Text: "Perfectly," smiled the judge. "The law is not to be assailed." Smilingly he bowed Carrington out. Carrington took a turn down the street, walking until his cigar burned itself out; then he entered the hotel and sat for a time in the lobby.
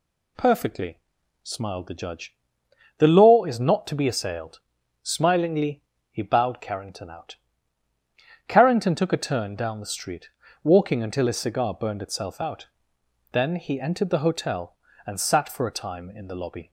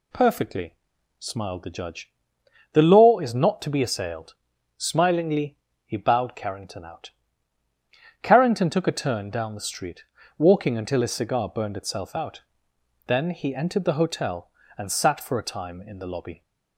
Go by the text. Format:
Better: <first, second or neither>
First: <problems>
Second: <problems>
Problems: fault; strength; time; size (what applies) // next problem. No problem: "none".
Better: neither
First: pauses between "Smilingly" and "he"; slight; at 5.8 s; 0.30 s long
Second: pauses between "Smilingly" and "he"; slight; at 5.5 s; 0.30 s long